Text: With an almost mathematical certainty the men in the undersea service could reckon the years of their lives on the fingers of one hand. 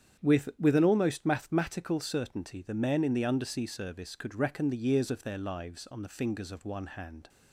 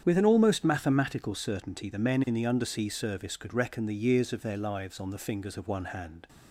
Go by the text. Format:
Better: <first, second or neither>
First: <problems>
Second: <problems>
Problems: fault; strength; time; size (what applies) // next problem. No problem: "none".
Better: second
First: starts louder than the rest; strong; until 1.3 s; 8.5 dB // says "With" twice; at 0.5 s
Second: starts louder than the rest; strong; until 1.0 s; 8.5 dB